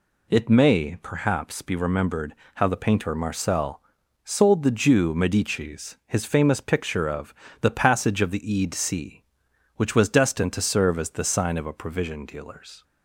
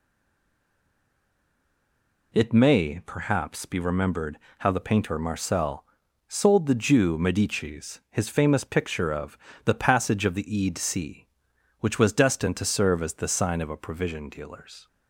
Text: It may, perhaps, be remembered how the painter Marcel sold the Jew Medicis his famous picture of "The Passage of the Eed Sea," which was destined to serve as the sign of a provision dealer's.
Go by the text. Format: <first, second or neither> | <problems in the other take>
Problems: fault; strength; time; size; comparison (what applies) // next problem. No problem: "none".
first | stays silent before the first word; until 2.3 s; 2.3 s long // pauses between "remembered" and "how"; slight; at 4.3 s; 0.20 s long; slight in the first // pauses between "Marcel" and "sold"; at 5.8 s; 0.42 s long; also in the first // pauses between "of" and "The"; slight; at 9.3 s; 0.28 s long; slight in the first